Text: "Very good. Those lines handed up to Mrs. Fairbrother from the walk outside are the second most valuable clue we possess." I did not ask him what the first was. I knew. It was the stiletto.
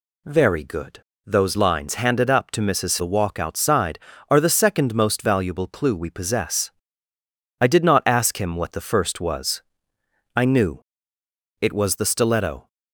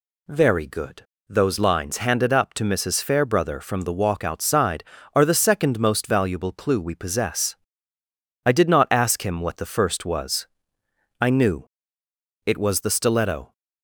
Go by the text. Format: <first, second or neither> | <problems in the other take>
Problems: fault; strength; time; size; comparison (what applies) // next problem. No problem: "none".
second | skips "Fairbrother from"; at 2.9 s